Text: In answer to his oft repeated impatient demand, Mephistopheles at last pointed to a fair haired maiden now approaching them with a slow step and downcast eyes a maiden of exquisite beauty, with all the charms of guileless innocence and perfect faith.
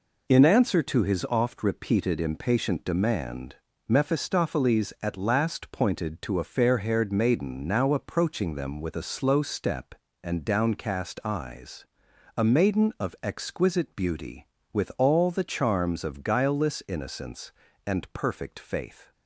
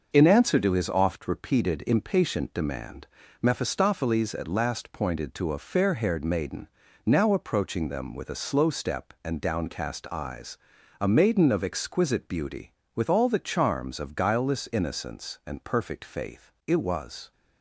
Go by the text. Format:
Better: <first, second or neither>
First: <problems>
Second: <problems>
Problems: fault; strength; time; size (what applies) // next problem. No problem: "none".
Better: first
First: pauses between "eyes" and "a"; noticeable; at 11.8 s; 0.50 s long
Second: starts louder than the rest; noticeable; until 1.1 s; 6 dB // pauses between "maiden" and "now"; at 6.6 s; 0.38 s long // pauses between "eyes" and "a"; at 10.5 s; 0.42 s long // goes on to say "It was"; noticeable; from 16.6 s on; 0.64 s long